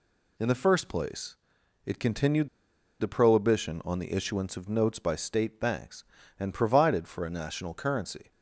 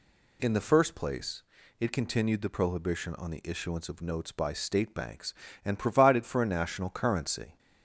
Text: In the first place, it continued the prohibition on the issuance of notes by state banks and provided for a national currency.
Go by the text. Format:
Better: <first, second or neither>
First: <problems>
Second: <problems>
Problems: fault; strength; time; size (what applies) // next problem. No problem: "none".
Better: second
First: pauses between "continued" and "the"; noticeable; at 2.4 s; 0.52 s long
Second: none